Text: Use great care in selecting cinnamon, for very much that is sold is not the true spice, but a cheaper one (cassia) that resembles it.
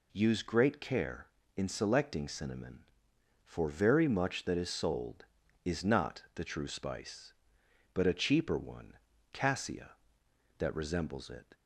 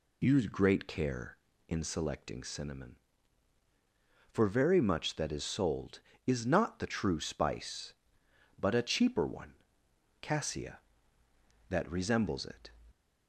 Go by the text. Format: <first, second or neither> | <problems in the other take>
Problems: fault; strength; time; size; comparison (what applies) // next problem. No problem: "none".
neither | none